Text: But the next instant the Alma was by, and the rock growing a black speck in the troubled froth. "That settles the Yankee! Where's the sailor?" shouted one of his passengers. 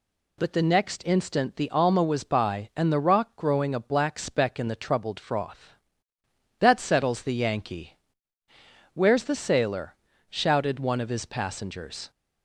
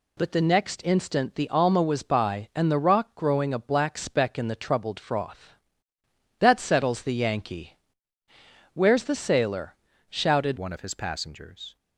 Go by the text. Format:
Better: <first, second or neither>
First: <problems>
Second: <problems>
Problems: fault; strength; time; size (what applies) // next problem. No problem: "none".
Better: first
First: none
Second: changes voice at "one"; from 10.5 s on; 1.2 s long